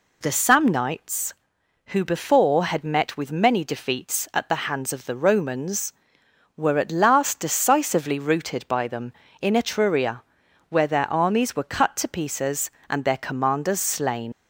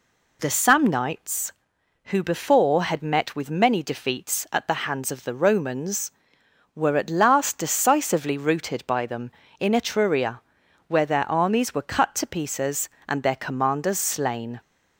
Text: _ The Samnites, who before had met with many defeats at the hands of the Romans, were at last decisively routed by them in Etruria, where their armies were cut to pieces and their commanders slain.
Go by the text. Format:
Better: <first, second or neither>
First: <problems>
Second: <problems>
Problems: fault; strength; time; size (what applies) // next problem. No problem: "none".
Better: second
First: leaves "slain" unfinished; at 14.3 s; 95 ms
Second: none